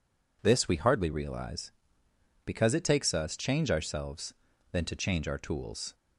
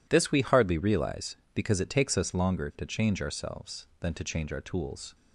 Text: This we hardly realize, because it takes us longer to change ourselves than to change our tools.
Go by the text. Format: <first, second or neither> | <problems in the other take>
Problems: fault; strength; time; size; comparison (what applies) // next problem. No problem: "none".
second | skips "longer to"; at 3.3 s